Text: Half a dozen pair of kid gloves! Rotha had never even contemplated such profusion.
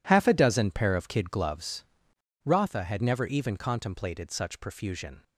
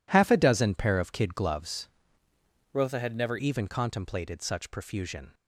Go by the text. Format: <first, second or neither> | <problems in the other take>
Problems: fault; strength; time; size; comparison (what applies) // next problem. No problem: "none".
first | changes voice from "Rotha" to "never"; from 2.7 to 3.3 s; 0.6 s long